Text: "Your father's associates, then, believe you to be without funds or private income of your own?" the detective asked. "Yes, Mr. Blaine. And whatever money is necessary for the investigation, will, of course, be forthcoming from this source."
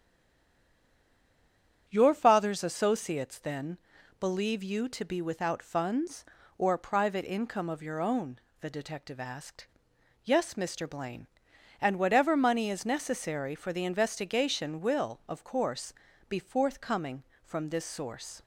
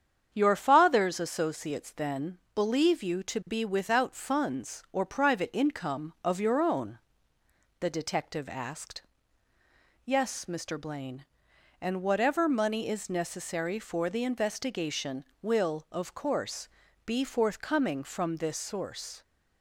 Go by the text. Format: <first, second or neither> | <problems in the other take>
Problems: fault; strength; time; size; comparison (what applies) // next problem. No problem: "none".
second | stays silent before the first word; noticeable; until 1.8 s; 1.8 s long // starts louder than the rest; strong; until 2.8 s; 8 dB; strong in the second